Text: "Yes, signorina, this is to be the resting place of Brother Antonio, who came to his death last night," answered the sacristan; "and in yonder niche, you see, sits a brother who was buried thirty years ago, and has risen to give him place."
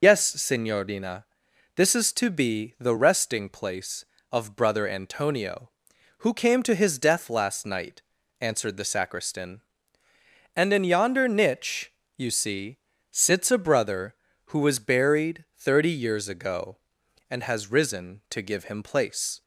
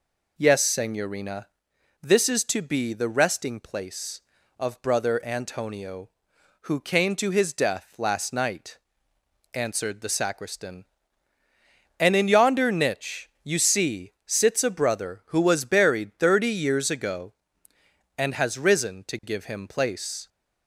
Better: second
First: loses the start of "Yes"; at 0.0 s; 45 ms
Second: none

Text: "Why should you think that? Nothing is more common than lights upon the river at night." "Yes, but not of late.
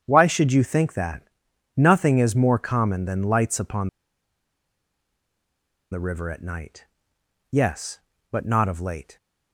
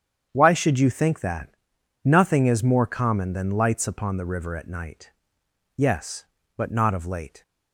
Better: second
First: starts louder than the rest; strong; until 1.0 s; 8 dB // pauses between "upon" and "the"; strong; at 3.8 s; 2.0 s long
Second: starts louder than the rest; strong; until 1.3 s; 8 dB

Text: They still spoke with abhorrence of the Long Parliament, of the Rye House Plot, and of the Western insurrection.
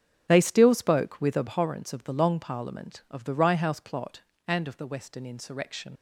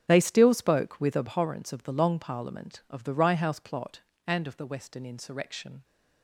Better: second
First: starts louder than the rest; strong; until 1.2 s; 7.5 dB // leaves "insurrection" unfinished; at 5.9 s; 95 ms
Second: starts louder than the rest; strong; until 1.0 s; 7.5 dB

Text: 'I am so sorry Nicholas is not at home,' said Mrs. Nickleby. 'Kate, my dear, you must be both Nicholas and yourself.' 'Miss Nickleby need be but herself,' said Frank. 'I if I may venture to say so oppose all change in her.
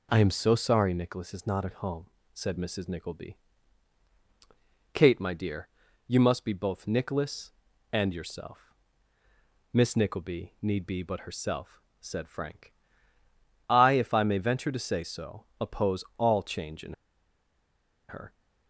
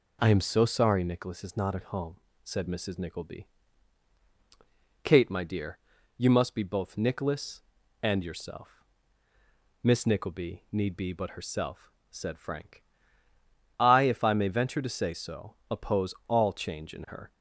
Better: second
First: pauses between "so" and "oppose"; slight; at 15.4 s; 0.16 s long // pauses between "in" and "her"; at 16.9 s; 1.1 s long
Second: pauses between "so" and "oppose"; slight; at 15.5 s; 0.16 s long

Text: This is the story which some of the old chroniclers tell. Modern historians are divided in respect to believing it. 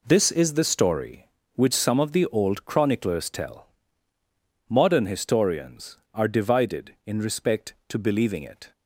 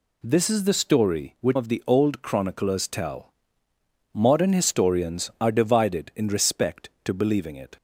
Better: first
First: none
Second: skips "some"; at 1.5 s

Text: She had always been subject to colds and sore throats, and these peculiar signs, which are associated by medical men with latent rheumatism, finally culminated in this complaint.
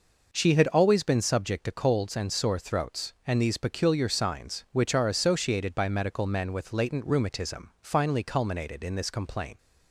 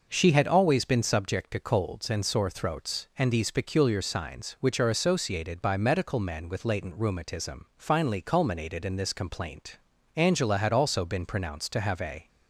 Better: first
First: none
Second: goes on to say "Angela had also been pronounced to have a"; strong; from 10.1 s on; 2.1 s long

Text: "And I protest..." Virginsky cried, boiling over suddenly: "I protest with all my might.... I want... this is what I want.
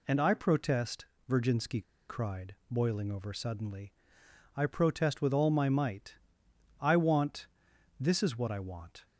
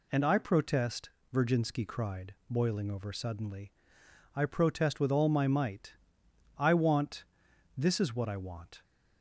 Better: second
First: pauses between "Virginsky" and "cried"; slight; at 1.8 s; 0.26 s long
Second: none

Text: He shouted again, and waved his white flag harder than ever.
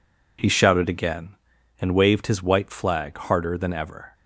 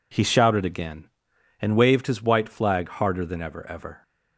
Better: first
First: none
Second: says "ever" twice; at 3.6 s

